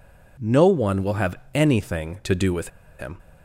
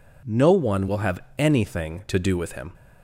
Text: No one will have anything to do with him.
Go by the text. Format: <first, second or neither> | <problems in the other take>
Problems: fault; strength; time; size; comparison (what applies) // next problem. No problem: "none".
second | pauses between "have" and "anything"; slight; at 1.3 s; 0.20 s long; slight in the second // pauses between "with" and "him"; slight; at 2.6 s; 0.31 s long